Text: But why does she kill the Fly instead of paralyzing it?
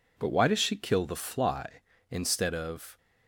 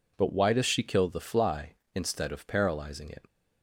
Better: second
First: stops before "paralyzing it"; at 2.9 s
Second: none

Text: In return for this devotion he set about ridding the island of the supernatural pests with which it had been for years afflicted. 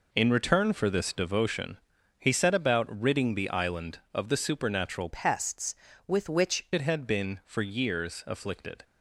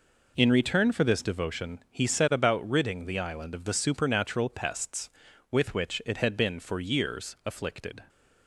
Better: second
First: pauses between "devotion" and "he"; at 1.7 s; 0.42 s long // changes voice from "pests" to "which"; from 5.1 to 6.6 s; 1.5 s long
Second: none

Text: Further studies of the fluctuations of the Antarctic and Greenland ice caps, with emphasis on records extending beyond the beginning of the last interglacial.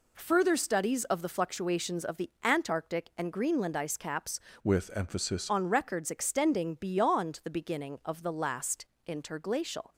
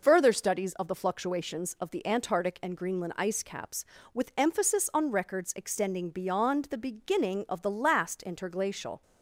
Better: second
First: changes voice from "with" to "emphasis"; from 4.6 to 5.4 s; 0.8 s long // pauses between "last" and "interglacial"; slight; at 8.8 s; 0.18 s long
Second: none

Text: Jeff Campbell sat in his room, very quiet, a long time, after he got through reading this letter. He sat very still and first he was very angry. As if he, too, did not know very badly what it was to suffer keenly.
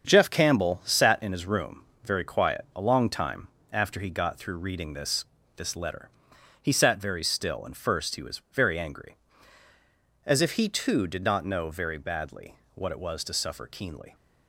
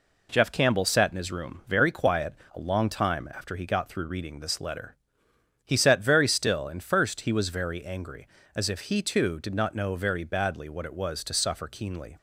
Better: second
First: starts louder than the rest; strong; until 1.1 s; 7.5 dB // says "this" twice; at 5.5 s // pauses between "badly" and "what"; slight; at 12.5 s; 0.20 s long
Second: none

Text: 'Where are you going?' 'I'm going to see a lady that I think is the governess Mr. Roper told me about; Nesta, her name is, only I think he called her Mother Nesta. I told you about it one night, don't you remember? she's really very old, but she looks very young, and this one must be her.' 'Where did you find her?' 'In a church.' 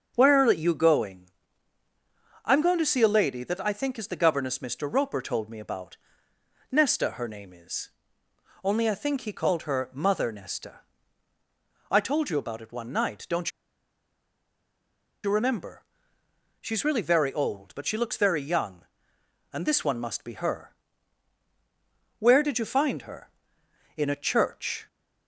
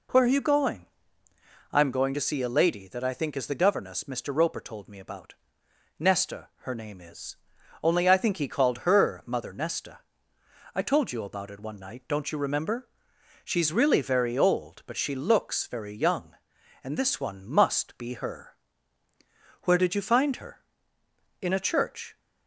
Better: second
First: starts louder than the rest; strong; until 1.1 s; 7 dB // pauses between "don't" and "you"; strong; at 13.4 s; 1.7 s long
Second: none

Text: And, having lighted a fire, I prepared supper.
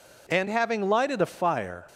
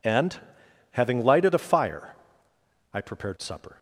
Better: second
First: stops before "I prepared supper"; at 1.8 s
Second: none

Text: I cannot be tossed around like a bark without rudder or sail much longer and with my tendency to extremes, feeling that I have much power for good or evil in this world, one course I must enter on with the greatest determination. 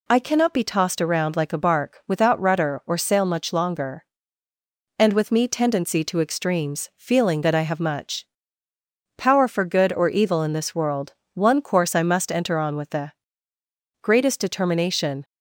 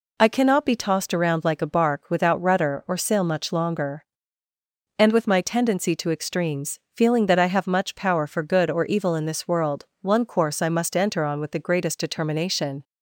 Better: second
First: says "me" for "my"; at 5.3 s // pauses between "much" and "power"; noticeable; at 8.2 s; 0.90 s long // pauses between "the" and "greatest"; noticeable; at 13.1 s; 0.90 s long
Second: none

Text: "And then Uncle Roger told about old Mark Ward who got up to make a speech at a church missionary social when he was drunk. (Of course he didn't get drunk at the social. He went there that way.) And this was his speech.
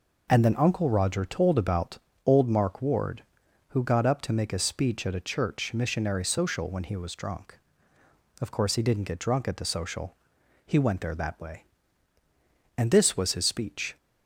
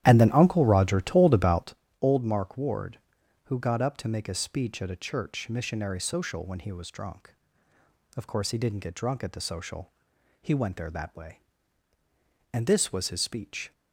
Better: first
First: pauses between "about" and "old"; slight; at 1.9 s; 0.28 s long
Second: starts louder than the rest; strong; until 1.8 s; 12 dB // pauses between "about" and "old"; slight; at 1.7 s; 0.28 s long

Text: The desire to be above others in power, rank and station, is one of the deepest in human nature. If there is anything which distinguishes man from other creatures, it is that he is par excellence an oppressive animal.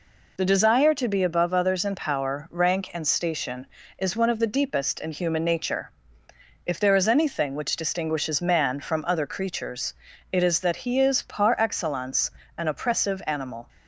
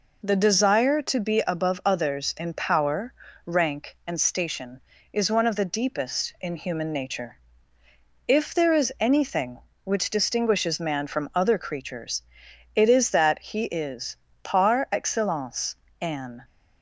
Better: first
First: pauses between "excellence" and "an"; slight; at 12.3 s; 0.26 s long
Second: pauses between "is" and "par"; slight; at 14.1 s; 0.30 s long // pauses between "excellence" and "an"; slight; at 15.7 s; 0.26 s long // stops before "oppressive animal"; at 16.4 s

